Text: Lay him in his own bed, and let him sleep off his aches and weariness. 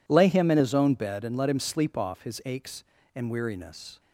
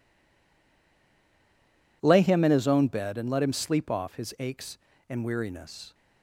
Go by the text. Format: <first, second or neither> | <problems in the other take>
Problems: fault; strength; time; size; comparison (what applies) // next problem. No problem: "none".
first | stays silent before the first word; noticeable; until 2.0 s; 2.0 s long